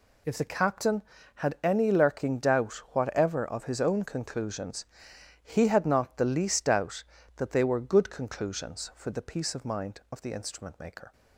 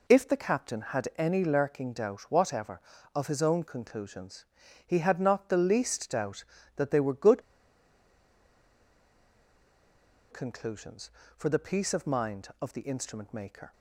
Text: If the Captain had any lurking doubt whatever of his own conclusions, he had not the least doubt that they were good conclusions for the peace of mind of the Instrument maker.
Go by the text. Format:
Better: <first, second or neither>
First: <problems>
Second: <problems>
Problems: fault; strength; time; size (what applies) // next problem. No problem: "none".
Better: first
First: none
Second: pauses between "good" and "conclusions"; strong; at 7.4 s; 2.9 s long